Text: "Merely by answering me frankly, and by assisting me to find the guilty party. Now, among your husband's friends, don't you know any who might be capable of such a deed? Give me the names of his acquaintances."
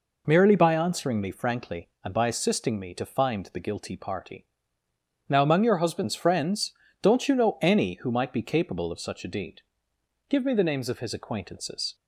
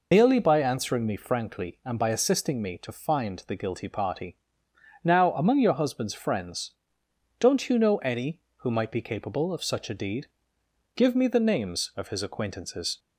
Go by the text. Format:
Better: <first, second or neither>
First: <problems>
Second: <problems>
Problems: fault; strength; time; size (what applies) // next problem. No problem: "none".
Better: first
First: none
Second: loses the start of "Merely"; at 0.1 s; 70 ms